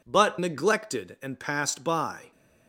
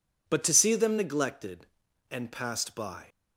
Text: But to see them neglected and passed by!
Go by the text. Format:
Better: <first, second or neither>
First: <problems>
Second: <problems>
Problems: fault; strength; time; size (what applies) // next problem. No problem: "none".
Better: second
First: skips "to see them"; at 0.4 s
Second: none